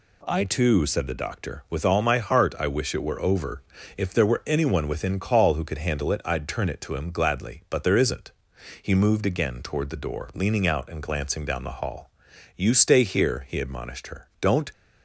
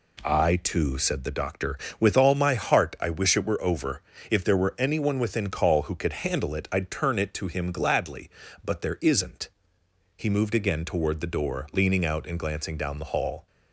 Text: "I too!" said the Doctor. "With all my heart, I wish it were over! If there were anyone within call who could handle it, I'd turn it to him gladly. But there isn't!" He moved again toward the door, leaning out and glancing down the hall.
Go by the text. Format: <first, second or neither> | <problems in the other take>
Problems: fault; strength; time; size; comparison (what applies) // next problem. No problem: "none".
second | goes on to say "You stay here he admonished her Don't"; strong; from 12.5 s on; 2.1 s long